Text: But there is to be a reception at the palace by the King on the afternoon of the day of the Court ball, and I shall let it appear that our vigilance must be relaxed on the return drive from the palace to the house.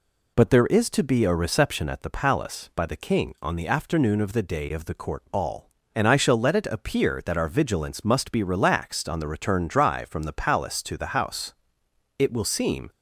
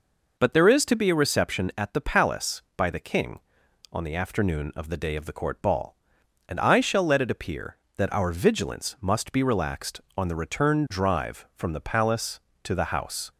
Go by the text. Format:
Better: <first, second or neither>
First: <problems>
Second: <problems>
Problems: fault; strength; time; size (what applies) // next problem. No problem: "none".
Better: second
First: goes on to say "It will seem"; noticeable; from 12.1 s on; 0.72 s long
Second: none